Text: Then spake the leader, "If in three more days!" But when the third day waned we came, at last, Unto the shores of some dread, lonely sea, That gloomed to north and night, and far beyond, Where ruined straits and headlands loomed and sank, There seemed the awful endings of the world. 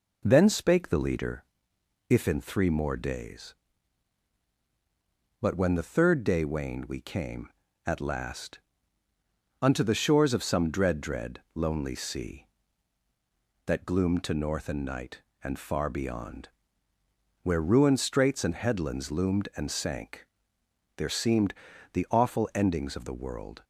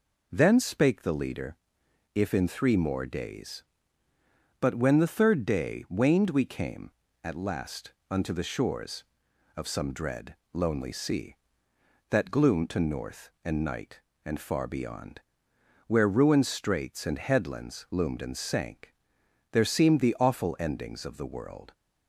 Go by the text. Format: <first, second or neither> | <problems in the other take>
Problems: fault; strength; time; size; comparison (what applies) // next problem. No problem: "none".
second | says "dread" twice; at 11.0 s // pauses between "seemed" and "the"; at 21.5 s; 0.38 s long